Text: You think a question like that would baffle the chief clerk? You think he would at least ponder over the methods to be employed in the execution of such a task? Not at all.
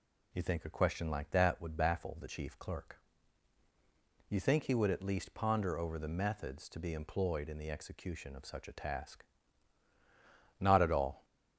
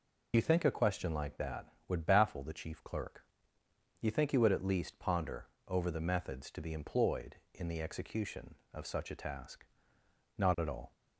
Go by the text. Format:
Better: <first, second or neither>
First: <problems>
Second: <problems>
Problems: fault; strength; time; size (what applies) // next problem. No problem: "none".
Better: first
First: none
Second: loses the start of "You"; at 0.3 s; 35 ms // pauses between "ponder" and "over"; slight; at 5.4 s; 0.20 s long